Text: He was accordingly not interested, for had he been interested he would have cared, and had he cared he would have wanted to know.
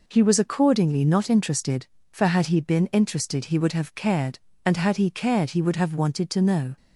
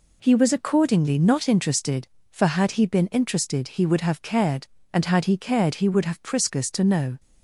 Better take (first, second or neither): first